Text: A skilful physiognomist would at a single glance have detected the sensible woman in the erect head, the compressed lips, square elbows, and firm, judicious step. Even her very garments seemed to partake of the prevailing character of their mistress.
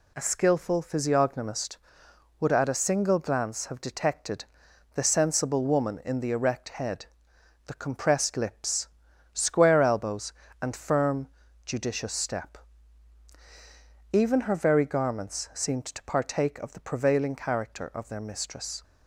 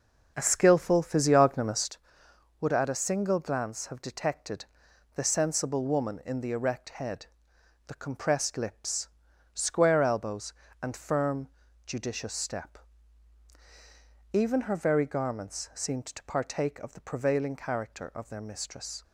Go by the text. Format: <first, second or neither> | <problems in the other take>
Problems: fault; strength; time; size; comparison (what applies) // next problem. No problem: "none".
first | starts louder than the rest; noticeable; until 2.0 s; 6 dB // pauses between "detected" and "the"; noticeable; at 4.6 s; 0.50 s long; noticeable in the first